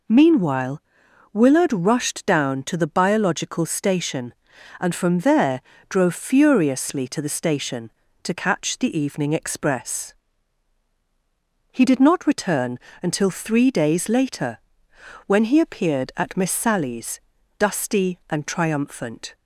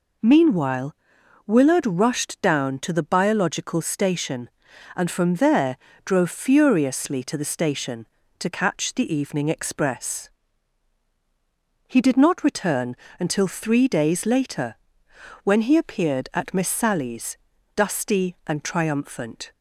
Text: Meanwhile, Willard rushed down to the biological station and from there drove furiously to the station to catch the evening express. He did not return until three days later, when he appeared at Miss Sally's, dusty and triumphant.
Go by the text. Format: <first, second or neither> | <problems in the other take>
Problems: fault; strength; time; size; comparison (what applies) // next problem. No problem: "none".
neither | pauses between "there" and "drove"; slight; the same in both // pauses between "return" and "until"; slight; the same in both